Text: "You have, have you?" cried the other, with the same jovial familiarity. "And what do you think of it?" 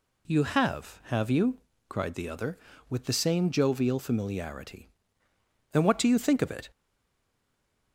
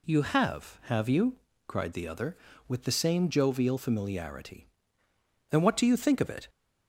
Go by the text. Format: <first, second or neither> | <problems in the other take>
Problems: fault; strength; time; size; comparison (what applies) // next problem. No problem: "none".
second | stays silent after the last word; noticeable; from 6.7 s on; 1.2 s long